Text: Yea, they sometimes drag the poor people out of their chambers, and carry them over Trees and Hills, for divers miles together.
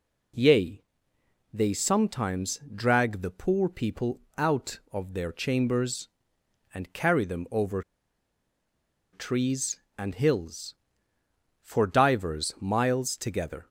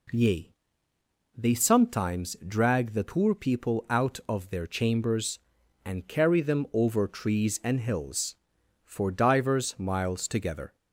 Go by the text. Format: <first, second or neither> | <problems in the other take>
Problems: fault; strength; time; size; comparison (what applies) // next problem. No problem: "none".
second | pauses between "sometimes" and "drag"; slight; at 2.5 s; 0.16 s long // pauses between "people" and "out"; slight; at 4.1 s; 0.18 s long // pauses between "over" and "Trees"; strong; at 7.8 s; 1.3 s long